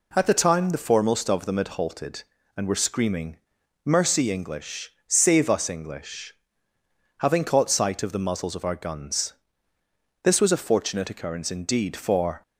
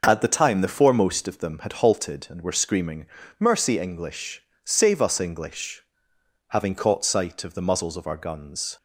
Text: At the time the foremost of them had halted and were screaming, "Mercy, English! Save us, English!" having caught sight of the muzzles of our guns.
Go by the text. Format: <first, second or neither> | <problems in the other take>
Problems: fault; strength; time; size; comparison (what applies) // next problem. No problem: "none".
second | goes on to say "This was a fortunate occurrence indeed for"; strong; from 10.2 s on; 2.1 s long